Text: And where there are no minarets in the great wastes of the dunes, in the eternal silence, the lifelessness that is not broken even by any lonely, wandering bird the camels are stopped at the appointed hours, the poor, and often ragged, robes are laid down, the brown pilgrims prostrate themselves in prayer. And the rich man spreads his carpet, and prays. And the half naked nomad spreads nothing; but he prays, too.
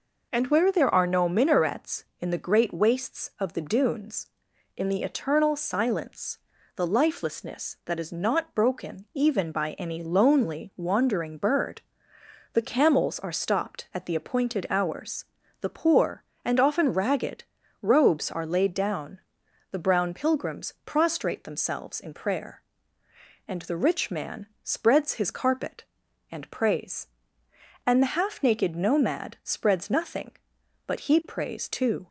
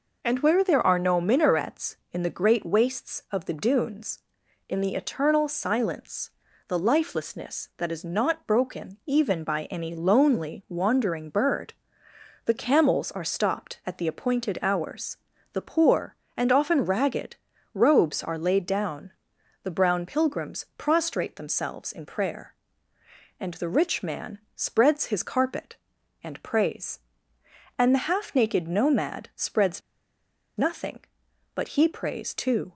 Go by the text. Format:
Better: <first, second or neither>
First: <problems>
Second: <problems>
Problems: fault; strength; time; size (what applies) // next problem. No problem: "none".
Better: first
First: pauses between "bird" and "the"; noticeable; at 11.8 s; 0.72 s long // pauses between "man" and "spreads"; slight; at 24.4 s; 0.16 s long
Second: pauses between "bird" and "the"; noticeable; at 11.7 s; 0.72 s long // pauses between "man" and "spreads"; slight; at 24.3 s; 0.16 s long // pauses between "spreads" and "nothing"; noticeable; at 29.8 s; 0.78 s long